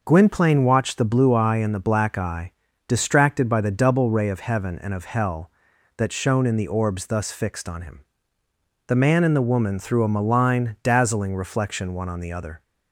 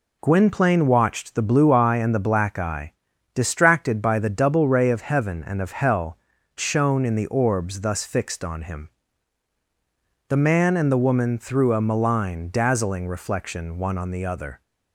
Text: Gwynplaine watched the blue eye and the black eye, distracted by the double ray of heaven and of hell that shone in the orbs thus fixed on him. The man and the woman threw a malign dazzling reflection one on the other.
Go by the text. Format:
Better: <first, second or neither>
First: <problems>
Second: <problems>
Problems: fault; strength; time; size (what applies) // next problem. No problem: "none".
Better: first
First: none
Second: skips "that"; at 6.3 s